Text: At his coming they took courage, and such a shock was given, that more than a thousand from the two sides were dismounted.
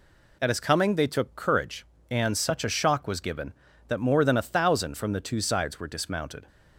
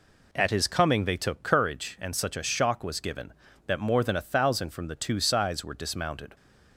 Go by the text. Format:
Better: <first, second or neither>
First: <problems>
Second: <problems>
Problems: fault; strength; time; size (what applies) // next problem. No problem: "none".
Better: neither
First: none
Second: none